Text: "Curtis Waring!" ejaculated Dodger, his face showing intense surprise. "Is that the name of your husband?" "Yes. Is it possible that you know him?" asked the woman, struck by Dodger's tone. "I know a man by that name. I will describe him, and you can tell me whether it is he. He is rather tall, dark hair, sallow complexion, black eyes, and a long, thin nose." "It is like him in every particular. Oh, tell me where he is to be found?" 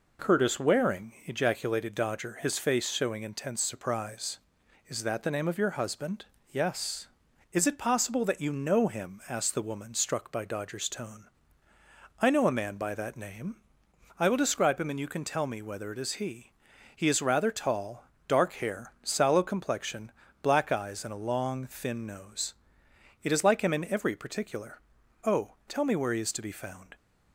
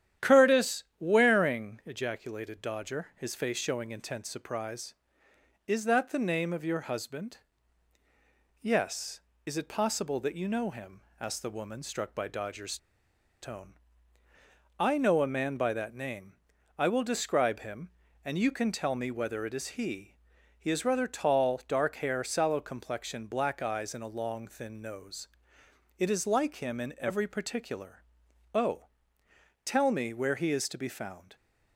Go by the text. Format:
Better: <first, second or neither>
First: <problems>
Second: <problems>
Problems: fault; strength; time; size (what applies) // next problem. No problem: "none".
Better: first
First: none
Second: starts louder than the rest; strong; until 1.3 s; 10.5 dB // pauses between "Curtis" and "Waring"; slight; at 0.8 s; 0.16 s long // pauses between "Dodger's" and "tone"; noticeable; at 12.7 s; 0.65 s long